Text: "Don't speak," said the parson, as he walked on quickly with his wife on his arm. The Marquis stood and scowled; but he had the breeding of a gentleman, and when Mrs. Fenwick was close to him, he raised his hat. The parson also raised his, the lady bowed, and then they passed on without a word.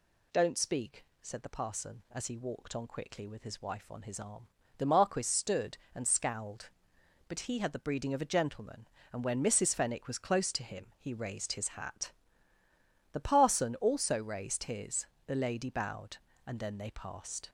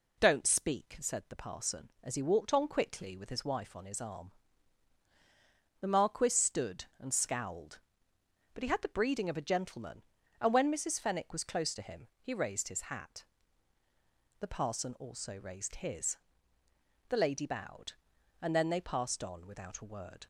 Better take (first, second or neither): second